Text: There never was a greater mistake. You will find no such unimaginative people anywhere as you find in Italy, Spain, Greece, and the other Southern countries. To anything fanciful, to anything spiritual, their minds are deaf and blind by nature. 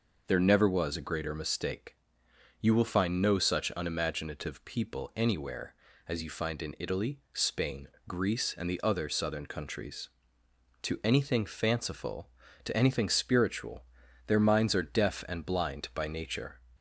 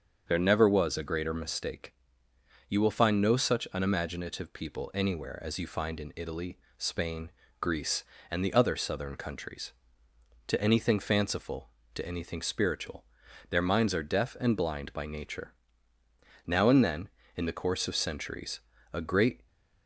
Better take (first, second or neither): first